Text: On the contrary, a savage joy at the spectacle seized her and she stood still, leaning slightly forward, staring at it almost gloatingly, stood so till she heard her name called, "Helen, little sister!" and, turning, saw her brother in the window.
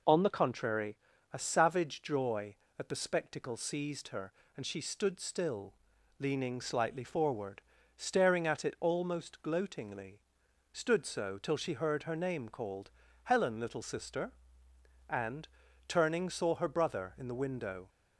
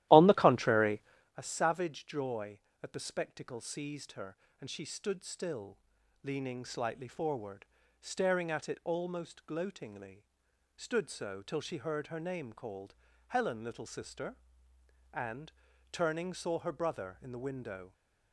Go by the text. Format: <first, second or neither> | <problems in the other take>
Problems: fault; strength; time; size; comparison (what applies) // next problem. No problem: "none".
first | starts louder than the rest; strong; until 1.4 s; 14.5 dB